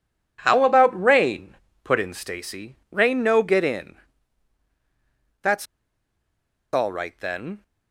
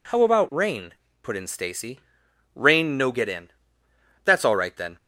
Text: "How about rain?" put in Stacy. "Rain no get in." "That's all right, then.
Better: second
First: pauses between "That's" and "all"; at 5.6 s; 1.0 s long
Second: none

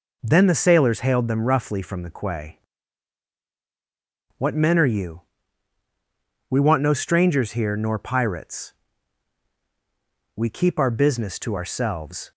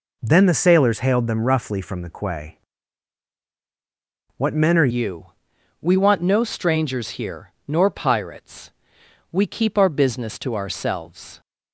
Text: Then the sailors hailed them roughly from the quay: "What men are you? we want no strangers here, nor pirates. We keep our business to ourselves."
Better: first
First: none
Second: changes voice at "you"; from 4.9 s on; 6.5 s long

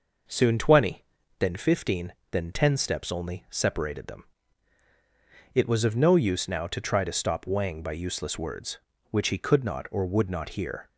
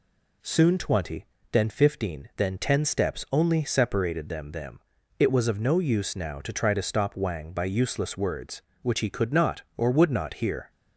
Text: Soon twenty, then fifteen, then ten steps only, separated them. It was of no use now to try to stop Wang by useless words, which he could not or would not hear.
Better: first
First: none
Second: says "them" twice; at 4.5 s

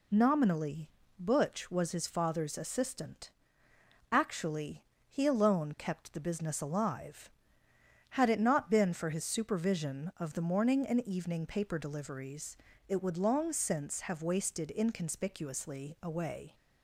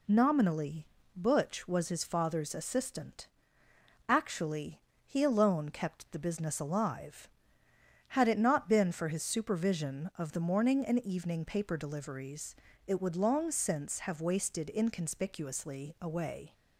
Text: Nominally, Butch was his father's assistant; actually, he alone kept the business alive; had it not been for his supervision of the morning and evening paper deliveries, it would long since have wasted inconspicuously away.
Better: neither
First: none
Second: none

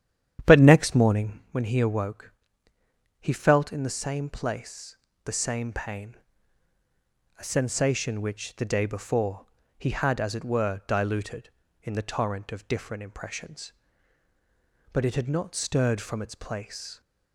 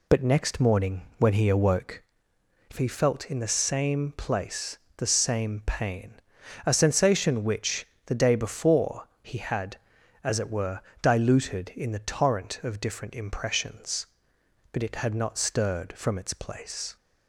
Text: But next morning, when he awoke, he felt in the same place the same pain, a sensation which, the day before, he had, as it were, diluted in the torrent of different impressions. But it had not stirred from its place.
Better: second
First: starts louder than the rest; strong; until 1.5 s; 10 dB // pauses between "place" and "the"; slight; at 4.9 s; 0.28 s long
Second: pauses between "place" and "the"; slight; at 4.7 s; 0.18 s long

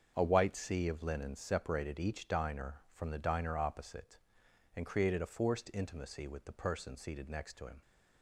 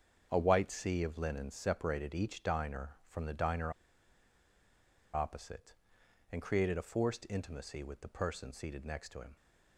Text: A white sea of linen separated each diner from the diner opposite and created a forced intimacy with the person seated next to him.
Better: first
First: starts louder than the rest; until 1.1 s; 6.5 dB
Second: starts louder than the rest; until 1.3 s; 6.5 dB // pauses between "diner" and "opposite"; strong; at 3.7 s; 1.4 s long

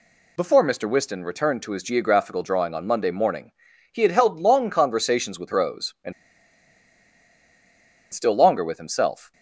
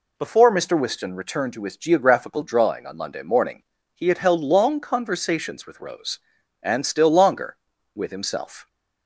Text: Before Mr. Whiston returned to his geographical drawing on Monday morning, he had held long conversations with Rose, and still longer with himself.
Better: second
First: pauses between "and" and "still"; strong; at 6.1 s; 2.0 s long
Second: none

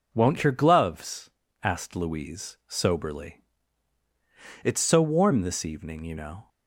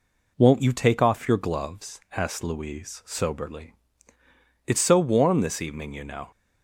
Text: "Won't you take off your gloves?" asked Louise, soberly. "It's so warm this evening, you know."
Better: second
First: skips "you take off"; at 0.4 s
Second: none

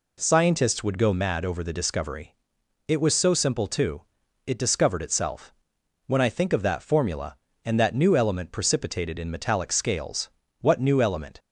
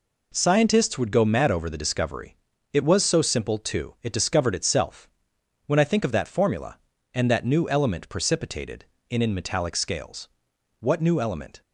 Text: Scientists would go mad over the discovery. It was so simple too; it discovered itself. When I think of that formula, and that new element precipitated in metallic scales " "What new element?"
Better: first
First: none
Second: says "in" twice; at 9.2 s

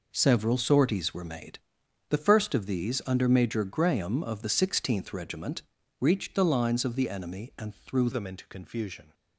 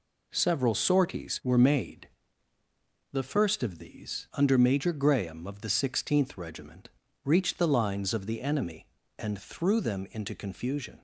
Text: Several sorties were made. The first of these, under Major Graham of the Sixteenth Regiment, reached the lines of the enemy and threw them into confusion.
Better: second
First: changes voice at "them"; from 8.1 s on; 1.0 s long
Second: none

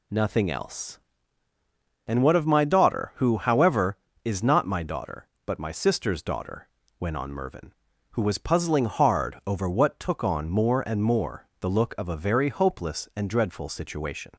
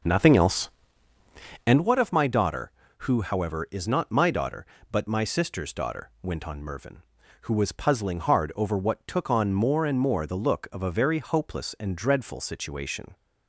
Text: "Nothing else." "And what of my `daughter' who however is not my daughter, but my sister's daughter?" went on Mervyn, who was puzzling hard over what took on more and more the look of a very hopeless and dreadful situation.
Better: first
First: none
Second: starts louder than the rest; noticeable; until 1.9 s; 6 dB

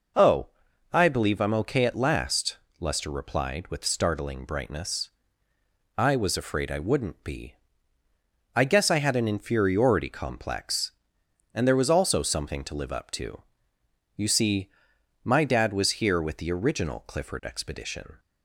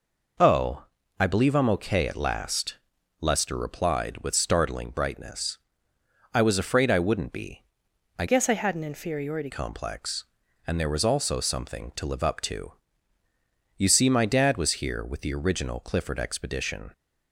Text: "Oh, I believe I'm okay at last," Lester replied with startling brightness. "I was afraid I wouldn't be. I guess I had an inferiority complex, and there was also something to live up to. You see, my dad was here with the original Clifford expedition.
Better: first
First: none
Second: changes voice from "guess" to "inferiority"; from 8.2 to 9.5 s; 1.3 s long

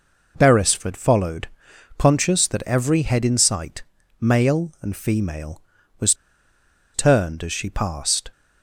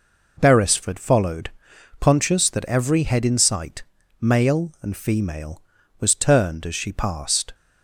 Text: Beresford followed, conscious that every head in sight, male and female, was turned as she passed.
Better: second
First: pauses between "was" and "turned"; noticeable; at 6.1 s; 0.80 s long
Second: none

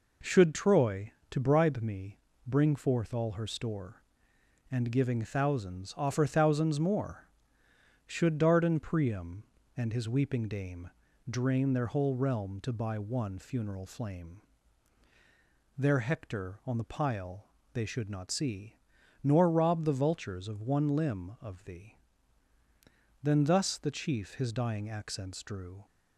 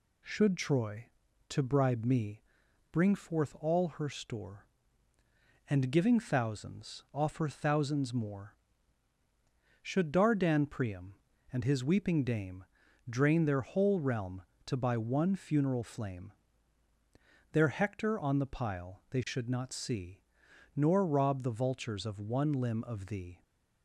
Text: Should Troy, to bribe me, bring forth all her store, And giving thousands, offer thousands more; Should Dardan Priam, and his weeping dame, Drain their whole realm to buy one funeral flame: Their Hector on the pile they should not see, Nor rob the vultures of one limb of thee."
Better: second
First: pauses between "pile" and "they"; slight; at 17.4 s; 0.26 s long // goes on to say "Then thus the chief his dying accents drew"; strong; from 23.2 s on; 2.6 s long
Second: none

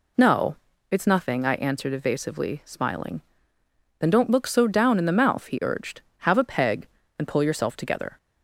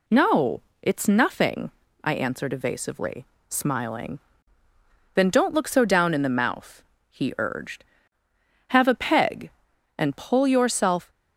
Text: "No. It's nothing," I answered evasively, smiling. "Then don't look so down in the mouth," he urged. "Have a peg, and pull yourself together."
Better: first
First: none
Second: stops before "together"; at 11.0 s

